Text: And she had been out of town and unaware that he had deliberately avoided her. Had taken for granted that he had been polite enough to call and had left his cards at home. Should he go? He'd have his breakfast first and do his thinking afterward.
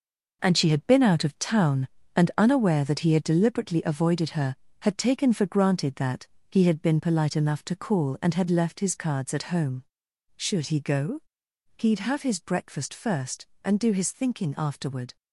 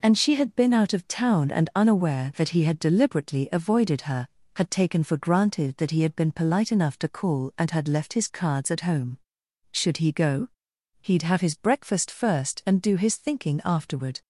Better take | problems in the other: second | gets quieter; strong; throughout; 8 dB // pauses between "that" and "he"; slight; at 6.2 s; 0.24 s long

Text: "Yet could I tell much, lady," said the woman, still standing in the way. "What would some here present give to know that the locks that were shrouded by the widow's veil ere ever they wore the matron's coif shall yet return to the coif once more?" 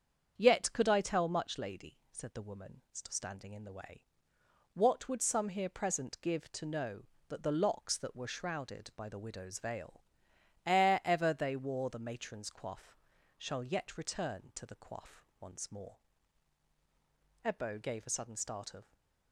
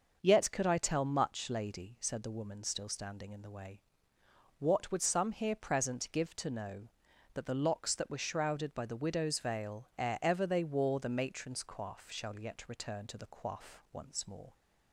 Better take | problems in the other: second | starts louder than the rest; strong; until 1.3 s; 7.5 dB; noticeable in the second // pauses between "veil" and "ere"; noticeable; at 10.0 s; 0.62 s long // pauses between "coif" and "shall"; at 12.9 s; 0.40 s long // pauses between "coif" and "once"; slight; at 15.2 s; 0.16 s long // goes on to say "Ebbo gave a sudden start of"; from 17.4 s on; 1.4 s long // stays silent after the last word; slight; from 18.8 s on; 0.5 s long

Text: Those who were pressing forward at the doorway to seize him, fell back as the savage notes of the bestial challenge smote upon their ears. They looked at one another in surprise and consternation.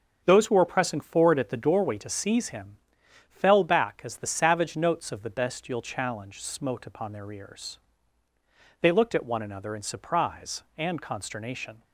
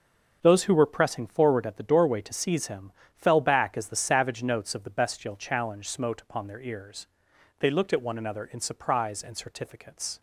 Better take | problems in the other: first | starts louder than the rest; until 1.4 s; 6 dB; also in the first // says "certificates" for "consternation"; at 9.3 s

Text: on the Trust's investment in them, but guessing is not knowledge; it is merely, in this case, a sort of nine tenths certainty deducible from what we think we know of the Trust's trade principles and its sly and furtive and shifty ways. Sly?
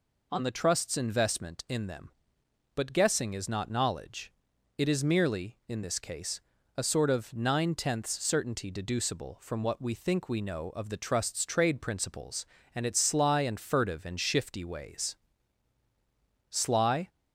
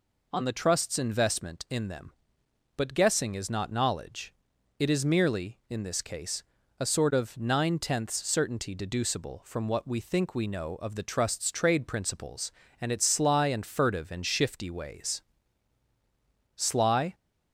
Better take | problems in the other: neither | none

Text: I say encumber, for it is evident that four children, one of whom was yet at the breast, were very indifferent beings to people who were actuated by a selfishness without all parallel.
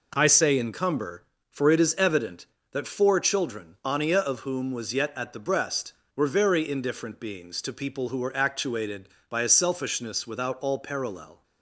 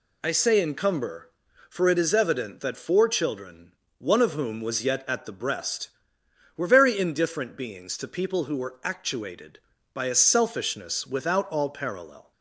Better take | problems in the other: second | says "ania" for "one"; at 3.8 s

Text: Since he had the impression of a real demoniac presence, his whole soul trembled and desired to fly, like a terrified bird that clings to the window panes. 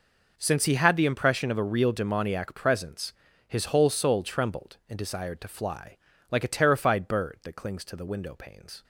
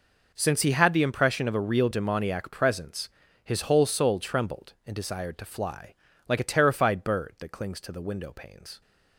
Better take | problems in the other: neither | none

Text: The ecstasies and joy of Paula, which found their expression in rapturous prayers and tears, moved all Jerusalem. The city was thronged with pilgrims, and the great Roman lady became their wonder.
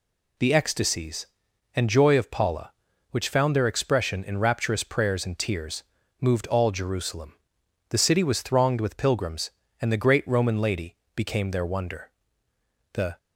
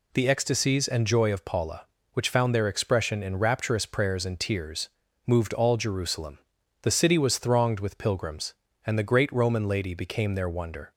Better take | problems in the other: second | pauses between "lady" and "became"; slight; at 10.9 s; 0.16 s long // goes on to say "The"; slight; from 12.9 s on; 0.24 s long

